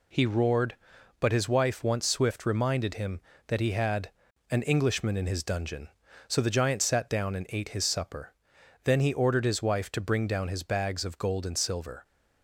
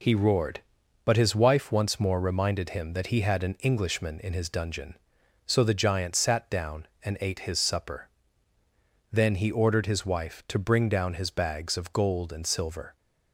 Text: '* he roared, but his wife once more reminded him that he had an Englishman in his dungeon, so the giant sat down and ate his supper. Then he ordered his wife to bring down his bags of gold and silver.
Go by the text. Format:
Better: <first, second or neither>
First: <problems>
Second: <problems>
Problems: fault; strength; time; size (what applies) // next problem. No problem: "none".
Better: second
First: says "swift" for "more"; at 2.0 s // pauses between "had" and "an"; at 4.0 s; 0.40 s long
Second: none